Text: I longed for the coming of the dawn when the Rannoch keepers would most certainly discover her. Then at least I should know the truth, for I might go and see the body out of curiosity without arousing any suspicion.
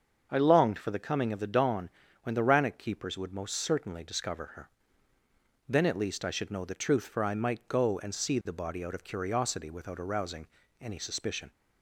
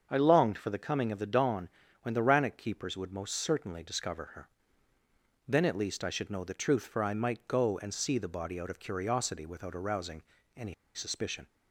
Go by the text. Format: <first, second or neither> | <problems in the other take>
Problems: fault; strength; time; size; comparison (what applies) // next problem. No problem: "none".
first | starts louder than the rest; until 1.1 s; 6.5 dB; also in the first // pauses between "dawn" and "when"; slight; at 1.7 s; 0.32 s long; slight in the first // pauses between "arousing" and "any"; slight; at 10.2 s; 0.32 s long; slight in the first // pauses between "any" and "suspicion"; slight; at 10.7 s; 0.20 s long